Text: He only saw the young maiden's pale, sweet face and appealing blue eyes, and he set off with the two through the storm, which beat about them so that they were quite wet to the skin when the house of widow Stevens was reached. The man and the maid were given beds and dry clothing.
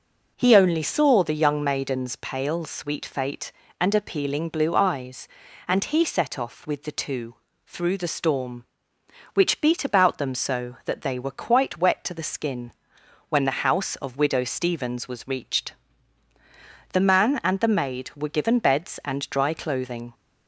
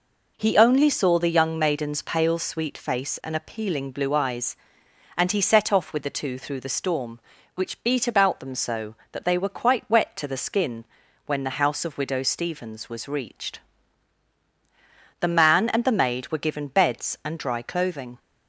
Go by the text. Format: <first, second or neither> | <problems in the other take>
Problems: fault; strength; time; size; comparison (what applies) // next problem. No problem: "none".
second | says "fate" for "face"; at 3.0 s // pauses between "two" and "through"; slight; at 7.3 s; 0.30 s long // pauses between "skin" and "when"; noticeable; at 12.7 s; 0.58 s long; also in the second